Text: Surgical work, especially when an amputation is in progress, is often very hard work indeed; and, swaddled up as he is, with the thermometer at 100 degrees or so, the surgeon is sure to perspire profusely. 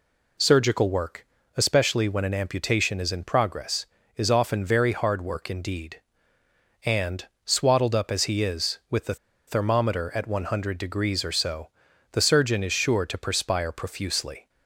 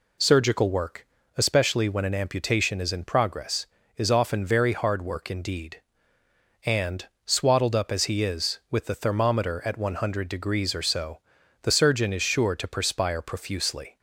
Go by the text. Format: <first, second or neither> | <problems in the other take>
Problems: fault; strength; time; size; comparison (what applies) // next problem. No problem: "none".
second | pauses between "the" and "thermometer"; slight; at 9.1 s; 0.31 s long